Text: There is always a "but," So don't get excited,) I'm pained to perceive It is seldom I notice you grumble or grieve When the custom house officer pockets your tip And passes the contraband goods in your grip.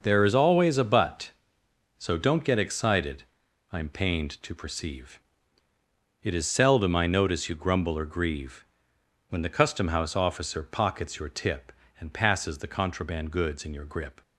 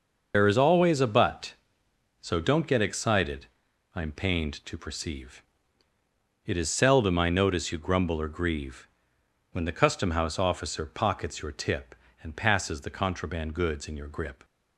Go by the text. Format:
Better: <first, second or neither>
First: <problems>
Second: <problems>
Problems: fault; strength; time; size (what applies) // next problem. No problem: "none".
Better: first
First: pauses between "perceive" and "It"; at 5.1 s; 1.0 s long // pauses between "grieve" and "When"; noticeable; at 8.6 s; 0.64 s long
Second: loses the start of "There"; at 0.3 s; 100 ms // pauses between "perceive" and "It"; at 5.4 s; 1.0 s long // pauses between "grieve" and "When"; noticeable; at 8.8 s; 0.64 s long